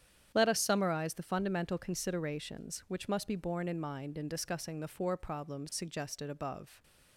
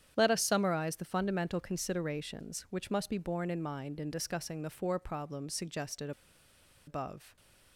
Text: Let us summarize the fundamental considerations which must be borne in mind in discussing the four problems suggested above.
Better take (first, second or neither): first